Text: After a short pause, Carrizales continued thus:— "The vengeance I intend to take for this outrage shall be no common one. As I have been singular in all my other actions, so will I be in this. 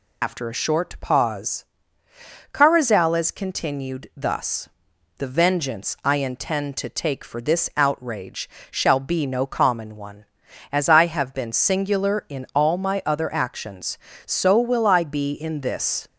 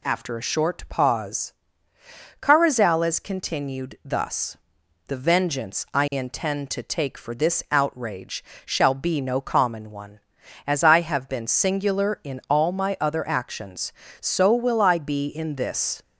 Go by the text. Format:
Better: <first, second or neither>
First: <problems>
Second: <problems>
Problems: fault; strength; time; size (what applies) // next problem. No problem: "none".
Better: second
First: loses the start of "After"; at 0.2 s; 60 ms // pauses between "outrage" and "shall"; slight; at 8.4 s; 0.22 s long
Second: pauses between "outrage" and "shall"; slight; at 8.4 s; 0.22 s long